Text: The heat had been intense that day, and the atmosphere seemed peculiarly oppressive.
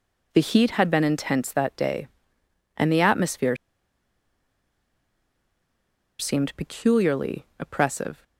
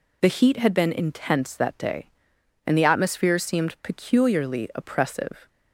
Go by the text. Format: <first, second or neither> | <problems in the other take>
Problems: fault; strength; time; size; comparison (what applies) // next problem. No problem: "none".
second | pauses between "atmosphere" and "seemed"; strong; at 3.5 s; 2.6 s long